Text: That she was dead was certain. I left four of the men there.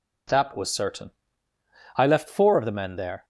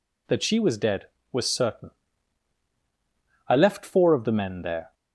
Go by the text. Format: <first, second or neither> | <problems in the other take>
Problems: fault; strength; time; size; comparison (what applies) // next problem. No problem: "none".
second | skips "she was dead"; at 0.5 s